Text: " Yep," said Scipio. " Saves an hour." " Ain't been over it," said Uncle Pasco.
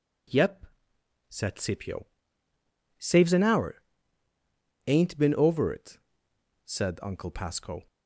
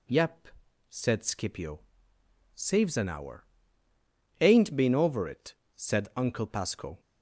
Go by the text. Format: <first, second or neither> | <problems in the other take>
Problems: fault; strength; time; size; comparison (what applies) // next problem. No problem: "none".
neither | none